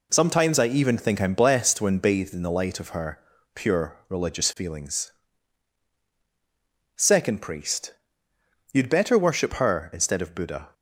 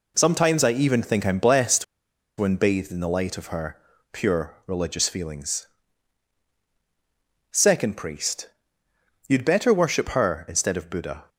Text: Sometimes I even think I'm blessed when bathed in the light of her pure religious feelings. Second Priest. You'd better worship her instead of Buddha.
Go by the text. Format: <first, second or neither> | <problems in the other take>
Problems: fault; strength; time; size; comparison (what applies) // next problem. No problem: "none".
first | pauses between "blessed" and "when"; noticeable; at 1.8 s; 0.53 s long // pauses between "her" and "pure"; slight; at 3.7 s; 0.34 s long; slight in the first